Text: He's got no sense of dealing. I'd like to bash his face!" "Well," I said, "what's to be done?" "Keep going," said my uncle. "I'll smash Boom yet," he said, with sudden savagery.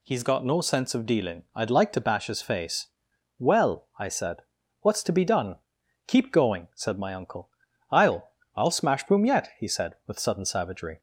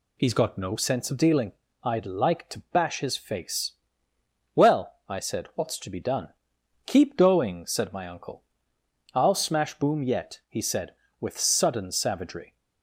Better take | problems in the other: second | says "I'll" twice; at 8.5 s

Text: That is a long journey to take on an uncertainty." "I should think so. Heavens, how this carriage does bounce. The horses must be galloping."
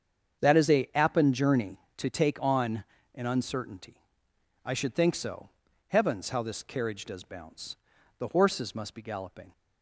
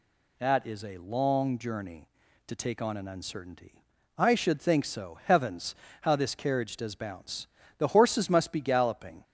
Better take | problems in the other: second | starts louder than the rest; strong; until 1.4 s; 7.5 dB // says "appen" for "long"; at 0.9 s // pauses between "on" and "an"; slight; at 2.8 s; 0.30 s long

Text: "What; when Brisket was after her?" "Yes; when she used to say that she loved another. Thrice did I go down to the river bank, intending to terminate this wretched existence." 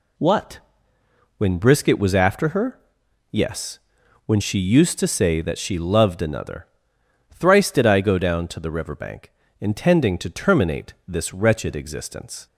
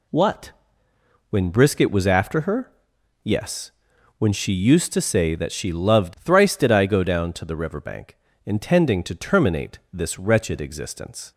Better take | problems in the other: first | skips "another"; at 6.1 s // pauses between "terminate" and "this"; slight; at 9.7 s; 0.16 s long; slight in the first

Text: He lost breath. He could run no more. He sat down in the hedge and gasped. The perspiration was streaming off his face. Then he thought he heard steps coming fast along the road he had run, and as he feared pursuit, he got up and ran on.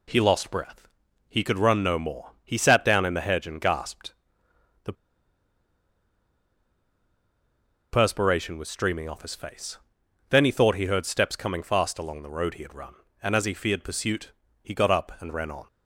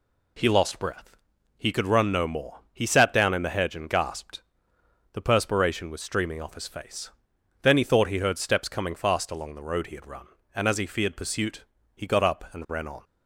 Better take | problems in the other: second | pauses between "The" and "perspiration"; strong; at 4.9 s; 2.9 s long

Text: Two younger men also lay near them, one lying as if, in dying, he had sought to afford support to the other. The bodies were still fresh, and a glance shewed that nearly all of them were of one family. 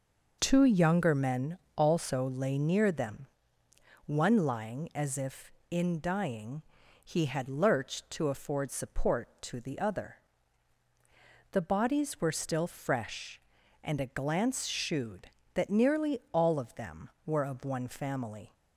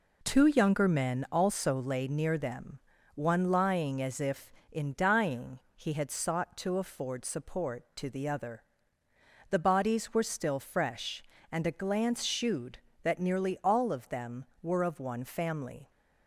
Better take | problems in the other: second | pauses between "men" and "also"; slight; at 1.5 s; 0.18 s long // says "lurched" for "sought"; at 7.4 s

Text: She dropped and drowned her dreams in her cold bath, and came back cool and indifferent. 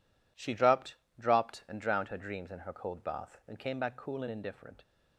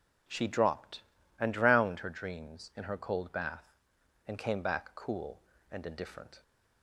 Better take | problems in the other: second | says "dropped" twice; at 1.1 s

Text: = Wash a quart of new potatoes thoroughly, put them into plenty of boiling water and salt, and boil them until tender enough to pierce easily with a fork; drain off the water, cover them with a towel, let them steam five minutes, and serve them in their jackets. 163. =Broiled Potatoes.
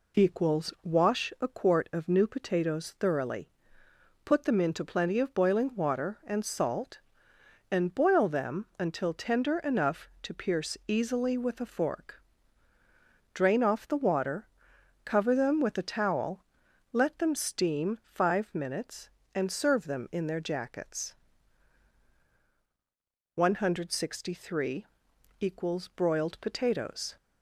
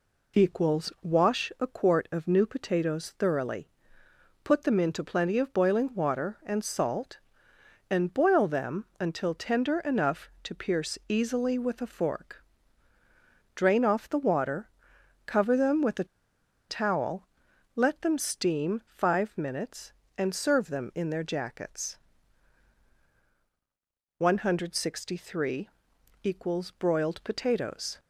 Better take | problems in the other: first | pauses between "a" and "towel"; noticeable; at 16.0 s; 0.64 s long

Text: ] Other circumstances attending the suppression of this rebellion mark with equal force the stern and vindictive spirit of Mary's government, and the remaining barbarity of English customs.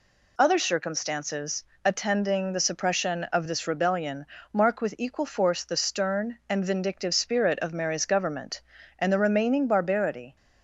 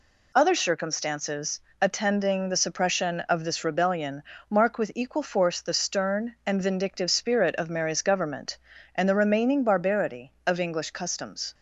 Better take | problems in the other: second | pauses between "circumstances" and "attending"; slight; at 1.6 s; 0.18 s long; slight in the second // pauses between "rebellion" and "mark"; slight; at 4.2 s; 0.26 s long; slight in the second // stops before "of English customs"; at 10.3 s

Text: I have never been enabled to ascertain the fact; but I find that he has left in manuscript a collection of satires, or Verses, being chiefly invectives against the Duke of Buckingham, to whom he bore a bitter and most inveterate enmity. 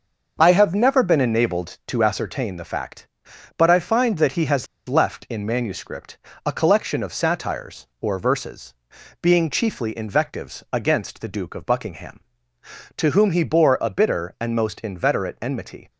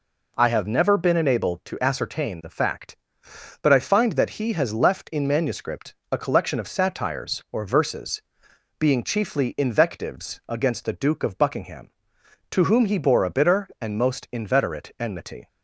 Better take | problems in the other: second | starts louder than the rest; until 1.4 s; 6 dB // pauses between "has" and "left"; slight; at 4.6 s; 0.22 s long // pauses between "manuscript" and "a"; slight; at 6.1 s; 0.28 s long; slight in the second

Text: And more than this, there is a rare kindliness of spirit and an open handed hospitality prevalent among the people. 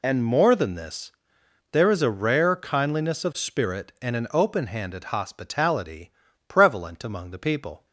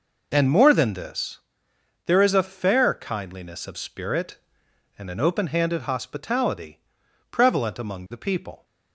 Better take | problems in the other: first | says "fair" for "rare"; at 2.4 s // pauses between "hospitality" and "prevalent"; noticeable; at 6.7 s; 0.52 s long; slight in the first

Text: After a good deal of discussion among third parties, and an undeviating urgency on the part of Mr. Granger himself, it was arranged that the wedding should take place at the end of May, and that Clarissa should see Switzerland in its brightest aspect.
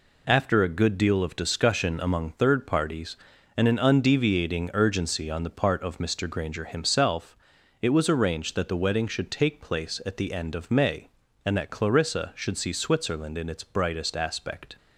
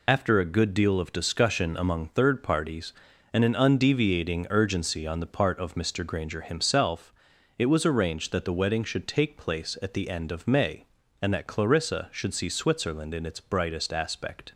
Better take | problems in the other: first | loses the start of "After"; at 0.0 s; 50 ms

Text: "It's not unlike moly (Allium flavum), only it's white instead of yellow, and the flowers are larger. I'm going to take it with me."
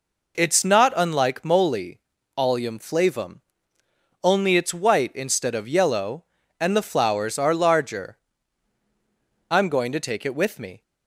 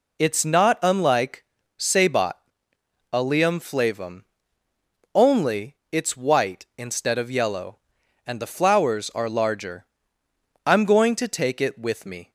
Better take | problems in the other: first | says "sabot" for "moly"; at 1.7 s

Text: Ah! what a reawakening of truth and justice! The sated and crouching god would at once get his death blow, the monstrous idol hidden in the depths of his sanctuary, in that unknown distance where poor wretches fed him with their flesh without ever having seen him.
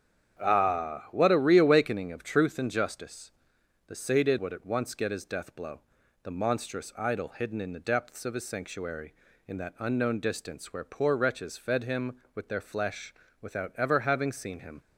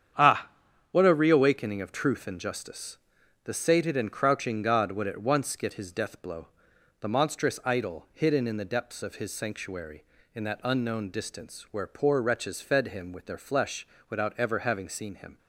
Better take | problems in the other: second | starts louder than the rest; strong; until 1.4 s; 8 dB; strong in the second // skips "and crouching god"; at 4.3 s // pauses between "flesh" and "without"; slight; at 13.1 s; 0.30 s long; slight in the second

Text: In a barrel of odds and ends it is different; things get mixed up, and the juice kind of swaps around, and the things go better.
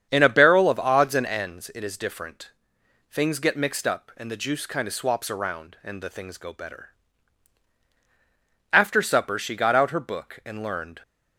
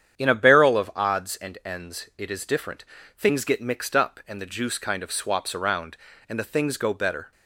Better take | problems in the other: second | starts louder than the rest; strong; until 1.1 s; 8 dB; strong in the second // goes on to say "After supper she got out her book and learned"; strong; from 8.7 s on; 2.3 s long

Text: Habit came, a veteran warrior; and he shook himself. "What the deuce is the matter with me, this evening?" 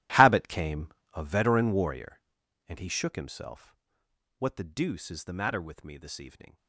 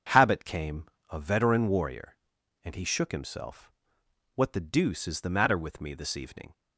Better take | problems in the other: second | gets quieter; strong; throughout; 17 dB // starts louder than the rest; strong; until 1.3 s; 15 dB; strong in the second

